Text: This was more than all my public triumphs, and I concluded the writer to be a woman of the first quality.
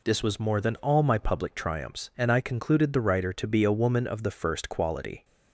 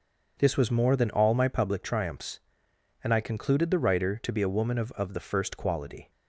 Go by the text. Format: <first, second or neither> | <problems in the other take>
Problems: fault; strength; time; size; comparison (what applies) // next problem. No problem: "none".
first | starts louder than the rest; noticeable; until 1.3 s; 6 dB // says "of" twice; at 4.9 s